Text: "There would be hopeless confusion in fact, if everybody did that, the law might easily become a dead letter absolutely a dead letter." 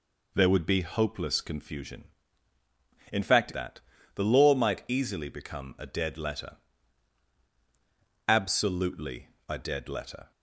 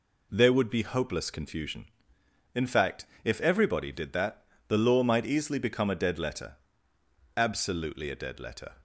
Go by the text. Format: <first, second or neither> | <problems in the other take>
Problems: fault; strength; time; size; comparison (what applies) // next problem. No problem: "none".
second | skips "if everybody did"; at 3.5 s // pauses between "letter" and "absolutely"; strong; at 6.5 s; 1.7 s long; noticeable in the second // pauses between "absolutely" and "a"; slight; at 9.2 s; 0.18 s long